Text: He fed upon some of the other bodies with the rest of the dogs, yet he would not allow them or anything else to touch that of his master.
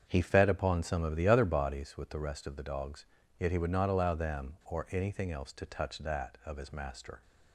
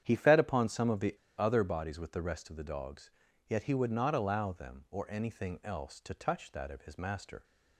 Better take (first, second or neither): first